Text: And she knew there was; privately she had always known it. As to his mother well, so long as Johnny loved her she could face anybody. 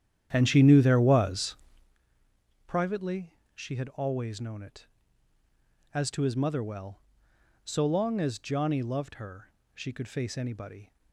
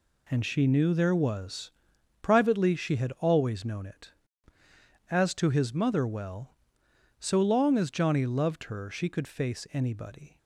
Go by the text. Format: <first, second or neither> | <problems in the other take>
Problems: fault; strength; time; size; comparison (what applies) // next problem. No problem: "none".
second | starts louder than the rest; strong; until 1.9 s; 10 dB // pauses between "privately" and "she"; slight; at 3.3 s; 0.20 s long // pauses between "her" and "she"; slight; at 9.4 s; 0.26 s long